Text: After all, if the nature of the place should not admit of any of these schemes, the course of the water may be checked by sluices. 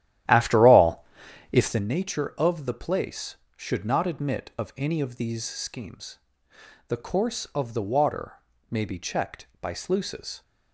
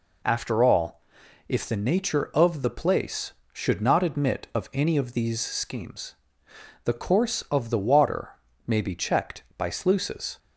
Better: second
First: starts louder than the rest; strong; until 2.0 s; 12 dB // pauses between "water" and "may"; slight; at 8.3 s; 0.36 s long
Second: pauses between "water" and "may"; slight; at 8.3 s; 0.36 s long

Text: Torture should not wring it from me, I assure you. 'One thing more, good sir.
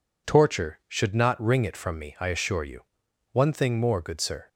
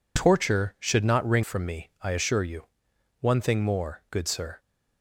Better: first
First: none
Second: skips "it"; at 1.4 s

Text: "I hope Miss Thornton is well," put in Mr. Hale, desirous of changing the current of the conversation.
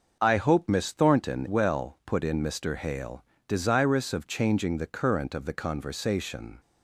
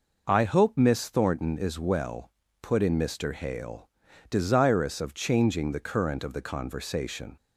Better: second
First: starts louder than the rest; noticeable; until 1.2 s; 6 dB // skips "is"; at 1.4 s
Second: none

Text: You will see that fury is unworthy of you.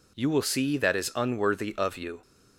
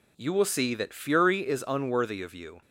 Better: second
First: skips "fury"; at 0.9 s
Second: none

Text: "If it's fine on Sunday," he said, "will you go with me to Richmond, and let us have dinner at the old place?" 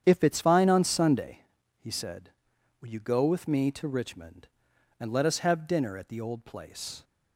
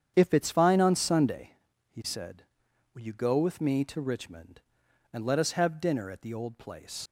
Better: first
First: starts louder than the rest; strong; until 1.0 s; 8.5 dB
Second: starts louder than the rest; strong; until 1.1 s; 8.5 dB // leaves "place" unfinished; at 7.0 s; 110 ms

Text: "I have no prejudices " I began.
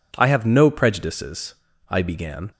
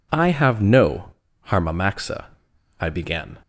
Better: first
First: none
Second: says "harmamaxa" for "prejudices"; at 1.4 s

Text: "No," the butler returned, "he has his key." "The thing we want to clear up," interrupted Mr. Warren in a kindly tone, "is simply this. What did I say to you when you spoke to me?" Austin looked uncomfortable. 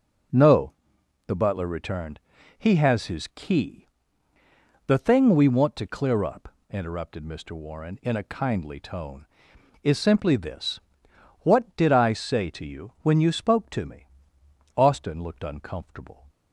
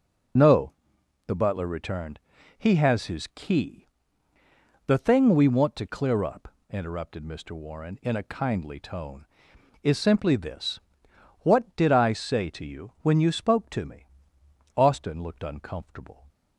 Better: first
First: none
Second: loses the start of "No"; at 0.3 s; 45 ms

